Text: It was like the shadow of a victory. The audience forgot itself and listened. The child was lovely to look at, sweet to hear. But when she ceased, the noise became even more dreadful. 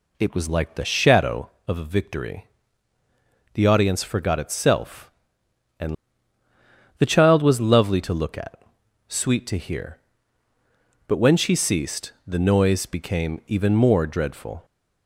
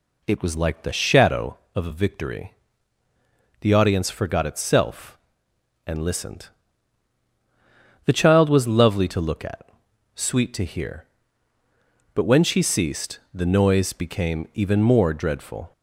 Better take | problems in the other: second | skips "listened"; at 6.4 s

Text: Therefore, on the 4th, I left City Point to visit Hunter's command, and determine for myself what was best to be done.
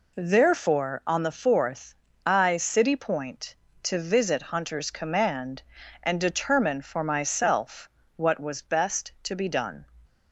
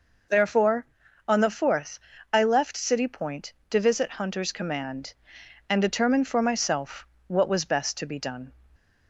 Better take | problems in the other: second | skips "left"; at 2.5 s // pauses between "myself" and "what"; slight; at 7.8 s; 0.27 s long; slight in the second

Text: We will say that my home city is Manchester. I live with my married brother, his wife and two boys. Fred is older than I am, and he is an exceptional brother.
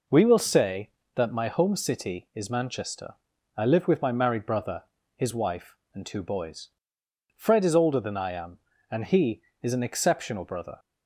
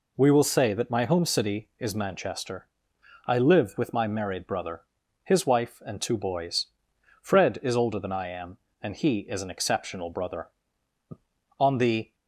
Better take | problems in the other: first | goes on to say "On the"; from 11.5 s on; 0.56 s long

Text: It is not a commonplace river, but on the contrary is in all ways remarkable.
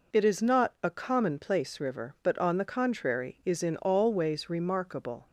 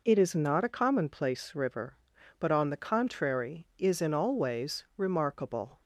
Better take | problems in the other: neither | none

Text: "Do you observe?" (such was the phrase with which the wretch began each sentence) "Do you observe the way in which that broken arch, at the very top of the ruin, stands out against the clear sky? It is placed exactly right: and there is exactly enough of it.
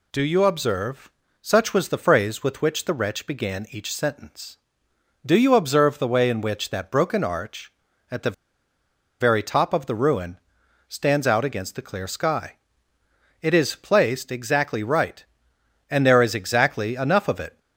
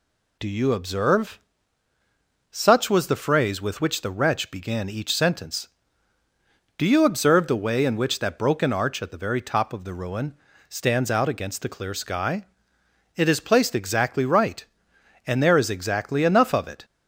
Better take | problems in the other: second | pauses between "the" and "very"; noticeable; at 8.3 s; 0.87 s long

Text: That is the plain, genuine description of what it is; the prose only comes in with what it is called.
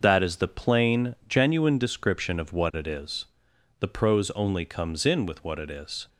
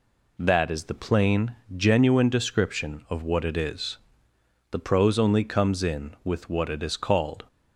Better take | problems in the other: second | starts louder than the rest; until 1.0 s; 6 dB // stops before "called"; at 6.0 s

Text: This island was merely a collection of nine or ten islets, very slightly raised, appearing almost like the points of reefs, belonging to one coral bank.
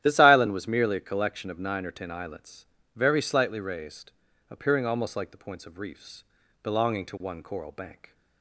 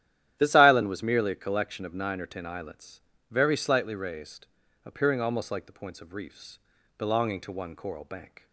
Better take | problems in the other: neither | starts louder than the rest; strong; the same in both

